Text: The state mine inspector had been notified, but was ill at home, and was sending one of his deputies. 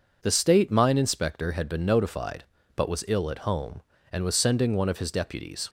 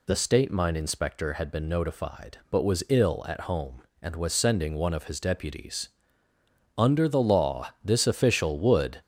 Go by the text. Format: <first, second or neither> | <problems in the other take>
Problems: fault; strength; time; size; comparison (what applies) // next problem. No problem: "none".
first | goes on to say "Under the law this official would"; strong; from 6.7 s on; 2.2 s long